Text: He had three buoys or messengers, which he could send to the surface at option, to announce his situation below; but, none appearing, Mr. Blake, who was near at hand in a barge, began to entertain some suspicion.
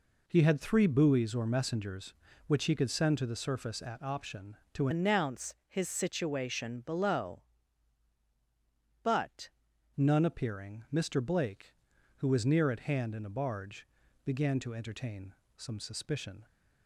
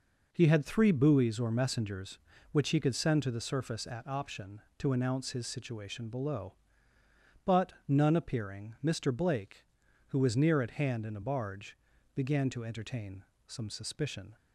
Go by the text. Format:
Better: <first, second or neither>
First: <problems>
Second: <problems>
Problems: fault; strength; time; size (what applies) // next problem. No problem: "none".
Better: second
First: changes voice from "announce" to "but"; from 4.9 to 9.4 s; 4.5 s long // pauses between "entertain" and "some"; slight; at 15.3 s; 0.24 s long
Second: pauses between "entertain" and "some"; slight; at 13.2 s; 0.24 s long